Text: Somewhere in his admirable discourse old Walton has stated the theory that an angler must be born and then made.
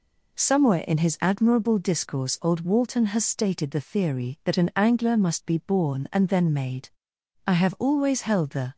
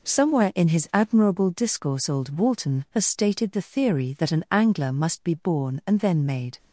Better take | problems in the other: second | goes on to say "I have always held the"; noticeable; from 7.4 s on; 1.2 s long

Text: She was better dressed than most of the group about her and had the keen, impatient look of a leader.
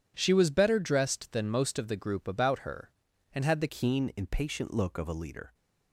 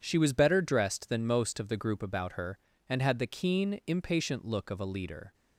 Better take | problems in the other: second | changes voice at "keen"; from 3.6 s on; 1.9 s long

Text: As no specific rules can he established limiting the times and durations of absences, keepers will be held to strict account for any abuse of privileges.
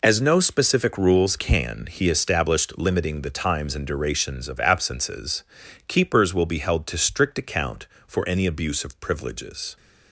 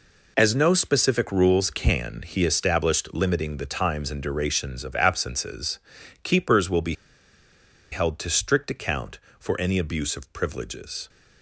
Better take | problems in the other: first | pauses between "be" and "held"; noticeable; at 6.9 s; 0.97 s long

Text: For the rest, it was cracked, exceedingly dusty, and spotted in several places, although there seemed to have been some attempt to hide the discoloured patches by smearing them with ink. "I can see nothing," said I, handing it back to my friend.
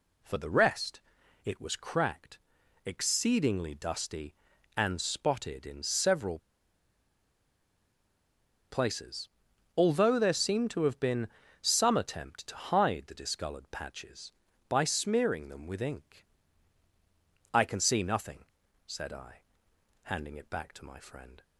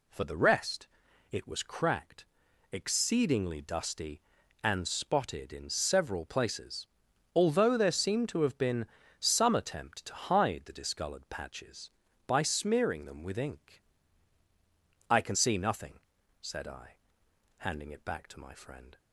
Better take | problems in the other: second | pauses between "several" and "places"; strong; at 6.3 s; 2.3 s long // pauses between "been" and "some"; slight; at 11.2 s; 0.32 s long; slight in the second

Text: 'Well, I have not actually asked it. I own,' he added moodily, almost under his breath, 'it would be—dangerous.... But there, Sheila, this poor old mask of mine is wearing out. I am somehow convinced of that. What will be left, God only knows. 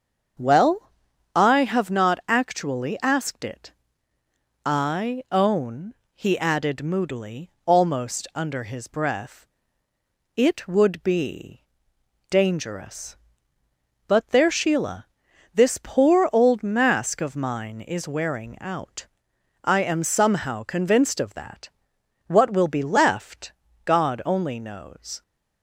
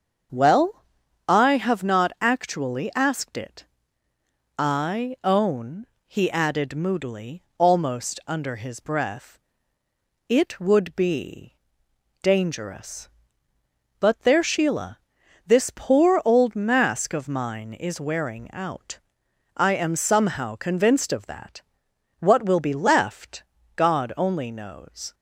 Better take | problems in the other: neither | starts louder than the rest; the same in both

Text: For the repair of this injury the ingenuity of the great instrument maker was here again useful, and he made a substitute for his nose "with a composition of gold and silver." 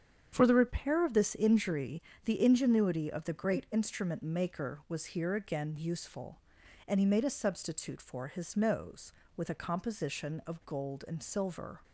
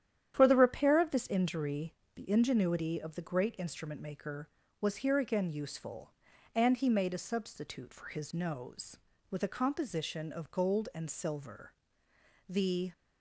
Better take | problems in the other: first | starts louder than the rest; strong; until 1.3 s; 10 dB; strong in the first // pauses between "injury" and "the"; slight; at 1.9 s; 0.22 s long; slight in the first // goes on to say "The"; slight; from 12.5 s on; 0.42 s long

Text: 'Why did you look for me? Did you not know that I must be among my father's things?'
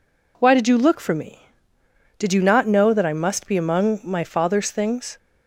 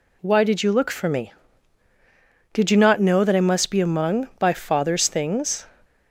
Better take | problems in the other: first | says "by" for "my"; at 4.3 s

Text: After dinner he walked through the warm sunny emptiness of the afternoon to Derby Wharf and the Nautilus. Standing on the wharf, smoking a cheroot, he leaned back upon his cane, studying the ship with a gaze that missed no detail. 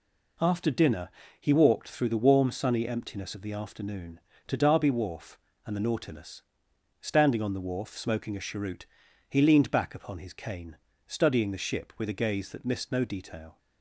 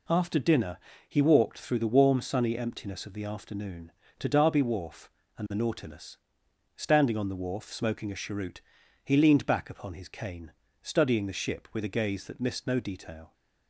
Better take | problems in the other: neither | pauses between "dinner" and "he"; slight; the same in both

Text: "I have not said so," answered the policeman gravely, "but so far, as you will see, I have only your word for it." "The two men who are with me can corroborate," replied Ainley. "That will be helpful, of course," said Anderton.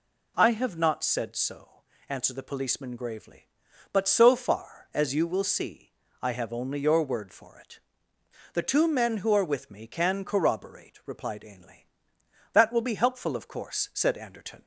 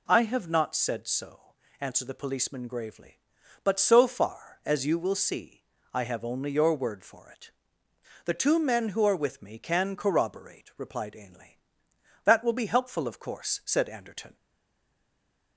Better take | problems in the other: first | stays silent after the last word; noticeable; from 14.3 s on; 1.2 s long

